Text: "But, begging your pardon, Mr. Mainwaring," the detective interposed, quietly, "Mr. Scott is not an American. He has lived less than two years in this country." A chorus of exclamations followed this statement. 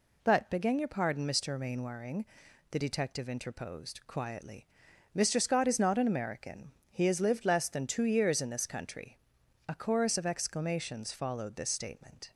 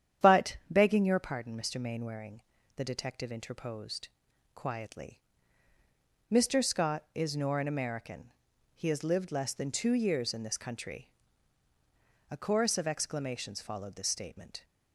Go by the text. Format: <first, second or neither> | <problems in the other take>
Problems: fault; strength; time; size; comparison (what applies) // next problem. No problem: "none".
first | starts louder than the rest; strong; until 1.3 s; 9.5 dB // says "nor" for "not"; at 7.3 s